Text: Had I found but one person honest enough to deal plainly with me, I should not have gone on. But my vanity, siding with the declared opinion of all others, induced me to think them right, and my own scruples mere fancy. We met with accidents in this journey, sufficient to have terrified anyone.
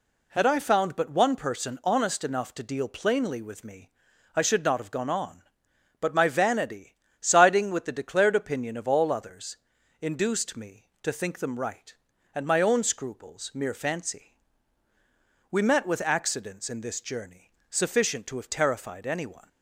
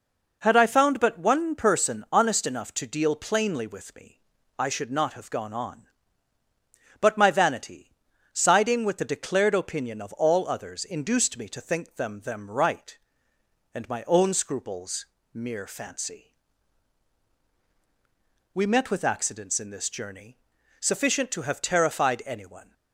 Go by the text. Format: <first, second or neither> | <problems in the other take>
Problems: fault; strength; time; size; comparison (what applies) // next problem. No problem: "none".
first | says "them" twice; at 12.2 s // pauses between "scruples" and "mere"; slight; at 15.0 s; 0.26 s long